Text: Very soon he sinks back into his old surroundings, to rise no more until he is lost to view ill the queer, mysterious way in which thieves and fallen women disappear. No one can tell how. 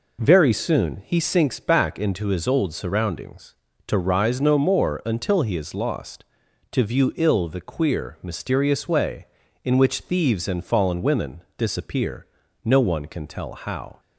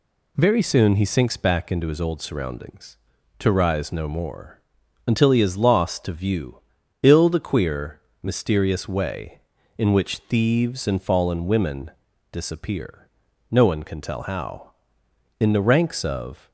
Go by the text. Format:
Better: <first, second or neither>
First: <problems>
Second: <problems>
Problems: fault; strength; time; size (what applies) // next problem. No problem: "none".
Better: first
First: pauses between "women" and "disappear"; slight; at 11.4 s; 0.16 s long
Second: pauses between "more" and "until"; noticeable; at 4.6 s; 0.46 s long // pauses between "view" and "ill"; at 6.5 s; 0.44 s long // pauses between "women" and "disappear"; at 11.9 s; 0.42 s long // goes on to say "In the ranks of"; noticeable; from 15.3 s on; 1.1 s long